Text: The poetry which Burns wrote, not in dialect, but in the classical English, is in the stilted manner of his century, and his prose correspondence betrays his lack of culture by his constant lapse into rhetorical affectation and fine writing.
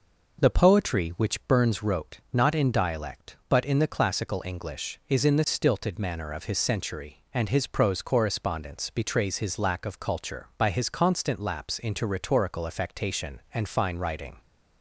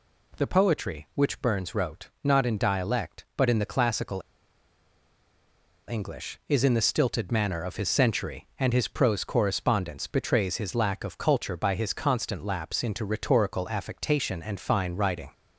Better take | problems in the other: first | pauses between "classical" and "English"; strong; at 4.1 s; 1.6 s long

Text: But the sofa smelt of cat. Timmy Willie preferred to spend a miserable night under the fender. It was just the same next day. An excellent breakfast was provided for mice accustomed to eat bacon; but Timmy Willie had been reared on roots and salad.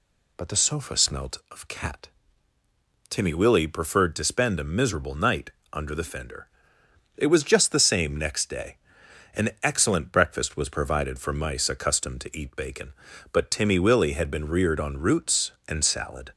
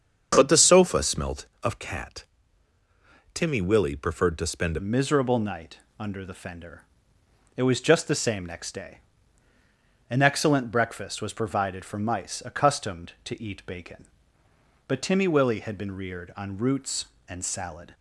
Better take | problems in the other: first | starts louder than the rest; until 1.3 s; 7 dB // changes voice at "miserable"; from 4.7 s on; 13.2 s long // pauses between "night" and "under"; slight; at 5.7 s; 0.22 s long; slight in the first

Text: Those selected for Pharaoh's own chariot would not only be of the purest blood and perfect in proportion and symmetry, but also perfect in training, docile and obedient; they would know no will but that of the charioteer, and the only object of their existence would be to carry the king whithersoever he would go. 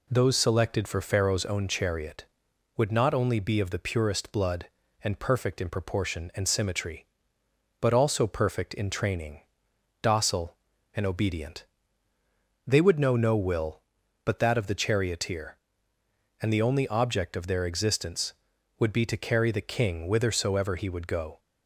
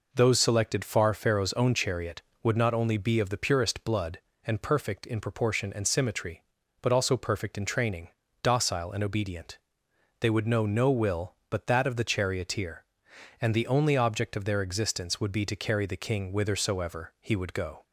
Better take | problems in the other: first | says "far" for "for"; at 0.8 s

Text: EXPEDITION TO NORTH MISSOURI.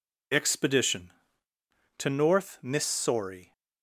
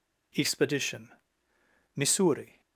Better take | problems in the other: first | skips "TO NORTH"; at 1.5 s

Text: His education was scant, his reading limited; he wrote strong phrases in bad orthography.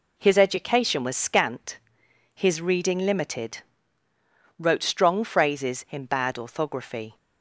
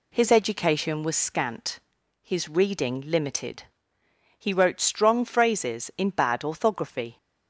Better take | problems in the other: second | skips "he"; at 4.0 s

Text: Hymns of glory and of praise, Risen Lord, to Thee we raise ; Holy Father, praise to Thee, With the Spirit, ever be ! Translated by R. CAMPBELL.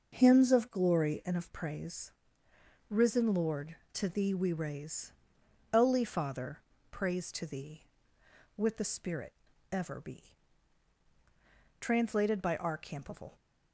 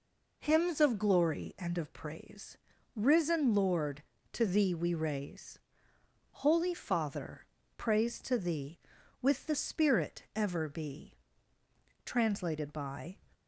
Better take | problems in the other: first | stops before "R CAMPBELL"; at 13.3 s

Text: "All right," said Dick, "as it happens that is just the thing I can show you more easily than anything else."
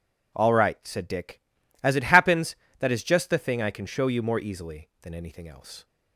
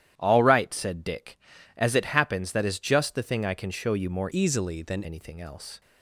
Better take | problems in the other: first | starts louder than the rest; strong; until 1.1 s; 11.5 dB // changes voice from "easily" to "than"; from 4.3 to 5.0 s; 0.7 s long

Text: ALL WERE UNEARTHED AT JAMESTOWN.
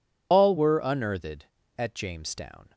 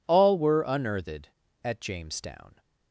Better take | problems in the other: second | loses the start of "ALL"; at 0.3 s; 75 ms

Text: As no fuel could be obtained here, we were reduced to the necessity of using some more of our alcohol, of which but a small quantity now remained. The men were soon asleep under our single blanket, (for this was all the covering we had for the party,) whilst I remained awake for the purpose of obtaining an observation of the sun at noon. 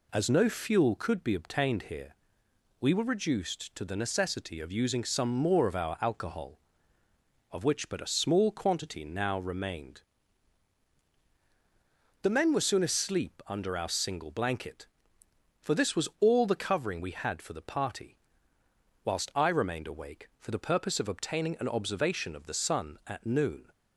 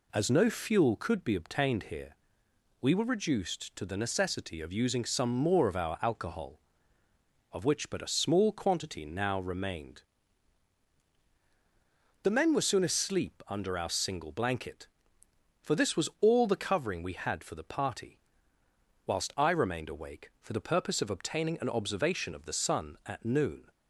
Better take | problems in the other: neither | none

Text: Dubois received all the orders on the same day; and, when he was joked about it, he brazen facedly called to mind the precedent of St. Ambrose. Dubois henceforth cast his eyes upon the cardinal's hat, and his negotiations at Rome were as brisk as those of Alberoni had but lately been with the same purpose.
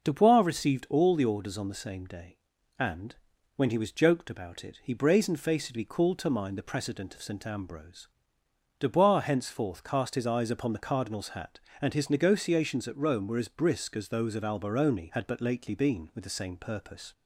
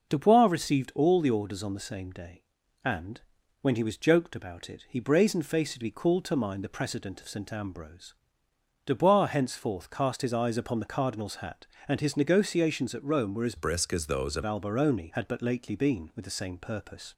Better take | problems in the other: first | changes voice from "brisk" to "of"; from 13.5 to 14.4 s; 0.9 s long

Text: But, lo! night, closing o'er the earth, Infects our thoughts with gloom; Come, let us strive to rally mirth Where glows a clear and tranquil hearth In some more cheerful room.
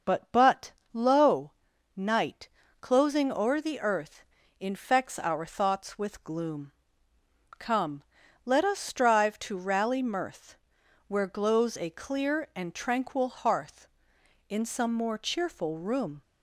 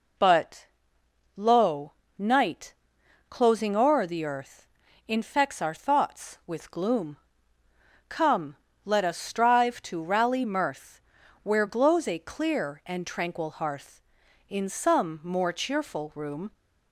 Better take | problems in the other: second | starts louder than the rest; until 1.2 s; 6 dB // says "But" twice; at 0.3 s // pauses between "mirth" and "Where"; noticeable; at 10.5 s; 0.52 s long; also in the second

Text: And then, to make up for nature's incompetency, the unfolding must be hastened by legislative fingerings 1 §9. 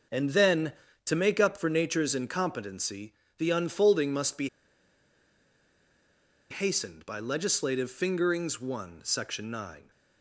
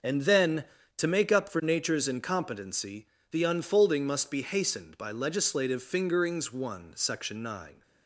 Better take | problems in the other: second | pauses between "be" and "hastened"; strong; at 4.4 s; 2.0 s long

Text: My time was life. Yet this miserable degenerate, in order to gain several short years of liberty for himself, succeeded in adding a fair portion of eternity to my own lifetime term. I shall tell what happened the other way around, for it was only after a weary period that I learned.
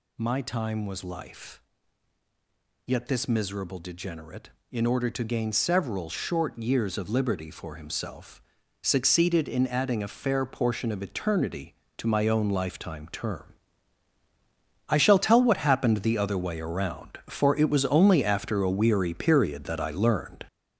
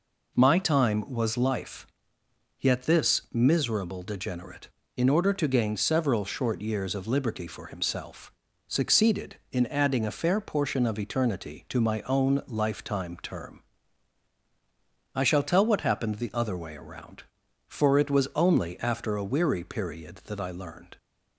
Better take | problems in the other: second | gets louder; throughout; 6.5 dB

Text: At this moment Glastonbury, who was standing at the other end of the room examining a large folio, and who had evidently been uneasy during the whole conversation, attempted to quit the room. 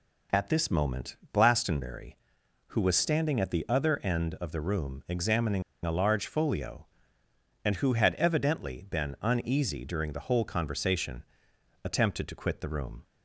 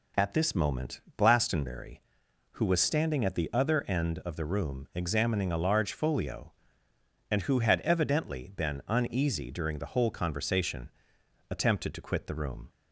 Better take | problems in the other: second | pauses between "moment" and "Glastonbury"; slight; at 1.1 s; 0.16 s long; slight in the second // pauses between "examining" and "a"; slight; at 5.6 s; 0.22 s long

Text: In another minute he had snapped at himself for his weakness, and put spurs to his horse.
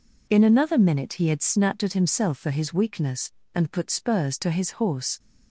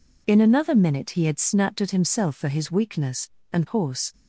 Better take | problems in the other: first | skips "put spurs to his"; at 3.6 s

